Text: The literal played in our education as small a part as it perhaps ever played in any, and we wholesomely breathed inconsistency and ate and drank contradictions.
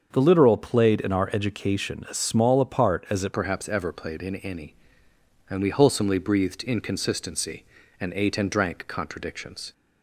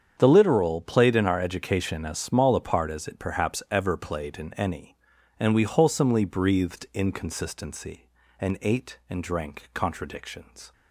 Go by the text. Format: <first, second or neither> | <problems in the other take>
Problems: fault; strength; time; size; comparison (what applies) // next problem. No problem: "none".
second | starts louder than the rest; until 1.1 s; 6.5 dB; strong in the second // changes voice at "perhaps"; from 3.3 s on; 6.4 s long